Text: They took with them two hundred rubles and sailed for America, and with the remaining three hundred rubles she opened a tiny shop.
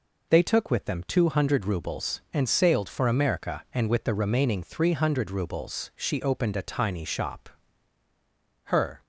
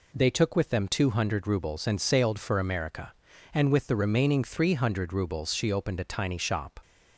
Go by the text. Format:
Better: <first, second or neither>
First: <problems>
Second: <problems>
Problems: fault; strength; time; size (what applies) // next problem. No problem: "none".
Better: second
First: goes on to say "Her"; slight; from 8.6 s on; 0.38 s long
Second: none